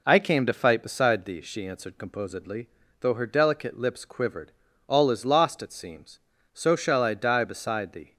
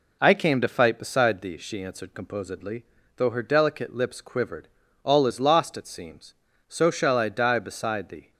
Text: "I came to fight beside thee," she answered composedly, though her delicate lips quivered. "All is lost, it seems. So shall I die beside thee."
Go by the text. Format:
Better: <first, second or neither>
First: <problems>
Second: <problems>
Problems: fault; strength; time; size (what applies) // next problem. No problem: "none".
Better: neither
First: none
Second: none